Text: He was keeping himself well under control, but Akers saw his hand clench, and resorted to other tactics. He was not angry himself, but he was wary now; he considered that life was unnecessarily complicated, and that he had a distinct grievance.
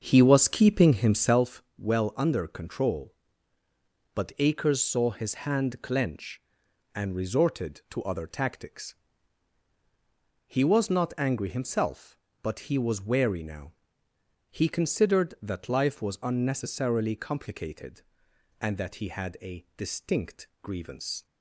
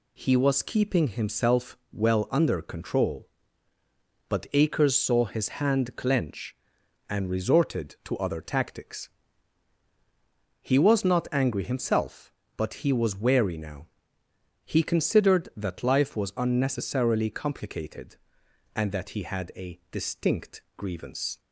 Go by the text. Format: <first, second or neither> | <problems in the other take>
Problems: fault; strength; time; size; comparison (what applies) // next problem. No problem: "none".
second | starts louder than the rest; until 1.5 s; 6.5 dB // pauses between "himself" and "well"; slight; at 1.6 s; 0.16 s long; slight in the second // pauses between "distinct" and "grievance"; slight; at 20.4 s; 0.16 s long; slight in the second